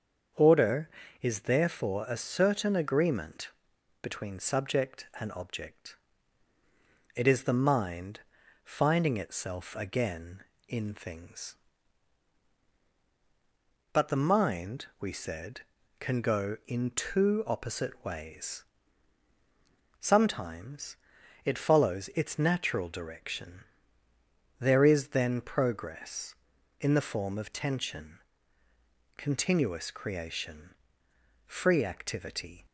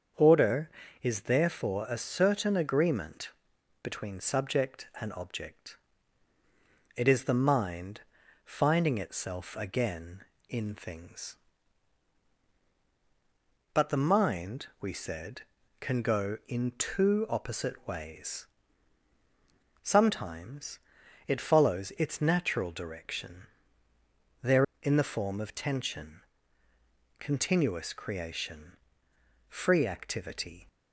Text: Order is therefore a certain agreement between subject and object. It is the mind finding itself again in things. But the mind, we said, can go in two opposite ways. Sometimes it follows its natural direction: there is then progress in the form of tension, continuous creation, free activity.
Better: first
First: starts louder than the rest; until 1.6 s; 7 dB // pauses between "agreement" and "between"; noticeable; at 3.4 s; 0.52 s long // pauses between "mind" and "finding"; at 8.2 s; 0.44 s long // pauses between "Sometimes" and "it"; noticeable; at 20.9 s; 0.48 s long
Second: starts louder than the rest; until 1.4 s; 7 dB // pauses between "agreement" and "between"; noticeable; at 3.2 s; 0.52 s long // pauses between "mind" and "finding"; at 8.0 s; 0.44 s long // pauses between "Sometimes" and "it"; noticeable; at 20.7 s; 0.48 s long // skips "is then progress"; at 24.7 s

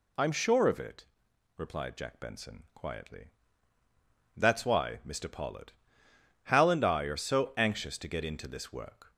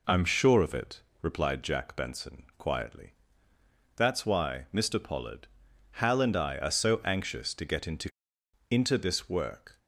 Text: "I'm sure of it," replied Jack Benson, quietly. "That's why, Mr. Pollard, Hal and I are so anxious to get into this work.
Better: first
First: none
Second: says "into" twice; at 8.6 s

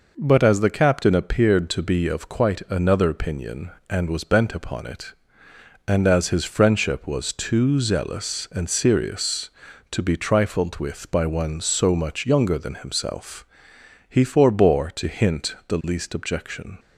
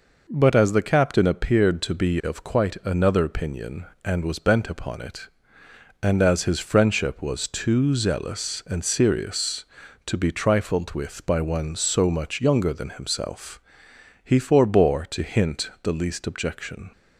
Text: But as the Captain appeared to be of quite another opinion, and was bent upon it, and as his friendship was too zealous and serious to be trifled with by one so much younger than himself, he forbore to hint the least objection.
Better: neither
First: none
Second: none

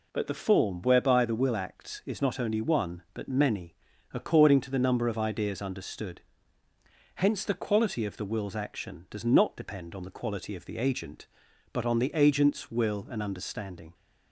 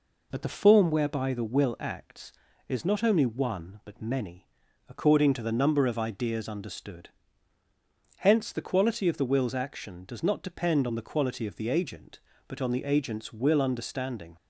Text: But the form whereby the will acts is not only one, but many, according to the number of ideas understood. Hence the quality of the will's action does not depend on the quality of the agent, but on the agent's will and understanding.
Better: first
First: none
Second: skips "and"; at 13.5 s

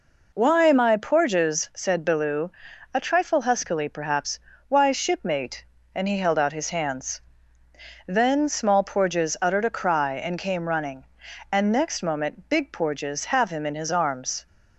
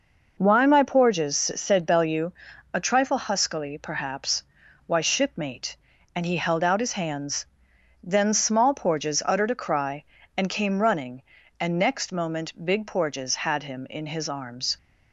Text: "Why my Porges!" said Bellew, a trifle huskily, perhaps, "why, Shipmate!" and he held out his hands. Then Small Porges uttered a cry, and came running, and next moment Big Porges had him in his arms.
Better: second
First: says "have" for "had"; at 13.2 s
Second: none

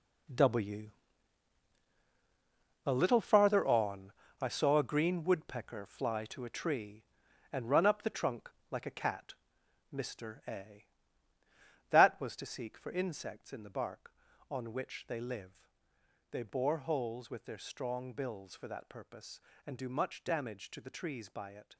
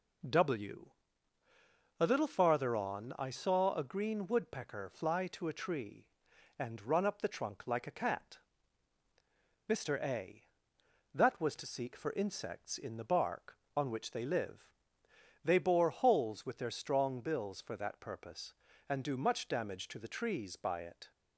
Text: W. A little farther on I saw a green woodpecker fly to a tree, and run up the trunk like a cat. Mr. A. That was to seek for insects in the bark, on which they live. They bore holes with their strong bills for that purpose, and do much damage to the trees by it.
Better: second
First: gets quieter; strong; throughout; 11 dB // pauses between "on" and "I"; slight; at 4.1 s; 0.28 s long // pauses between "trunk" and "like"; slight; at 8.4 s; 0.22 s long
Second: none

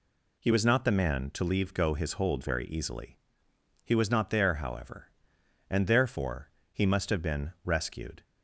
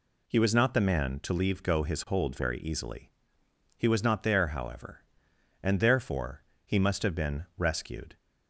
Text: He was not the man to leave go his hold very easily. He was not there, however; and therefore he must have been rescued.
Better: neither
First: pauses between "therefore" and "he"; slight; at 6.4 s; 0.24 s long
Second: pauses between "therefore" and "he"; slight; at 6.4 s; 0.24 s long

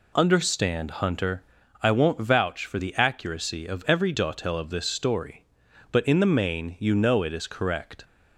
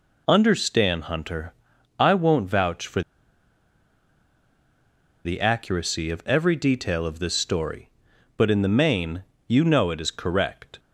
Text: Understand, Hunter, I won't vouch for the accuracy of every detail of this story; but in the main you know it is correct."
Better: first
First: none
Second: pauses between "for" and "the"; strong; at 3.0 s; 2.2 s long // pauses between "main" and "you"; slight; at 9.2 s; 0.26 s long

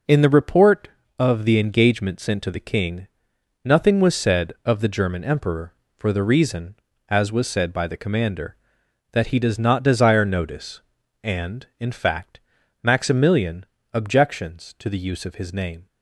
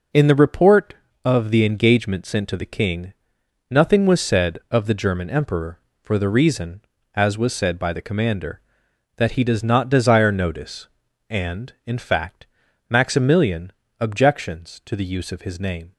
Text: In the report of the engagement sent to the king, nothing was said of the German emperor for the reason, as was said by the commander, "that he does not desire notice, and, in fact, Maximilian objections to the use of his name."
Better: neither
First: pauses between "Maximilian" and "objections"; slight; at 13.6 s; 0.30 s long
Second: pauses between "Maximilian" and "objections"; slight; at 13.7 s; 0.30 s long

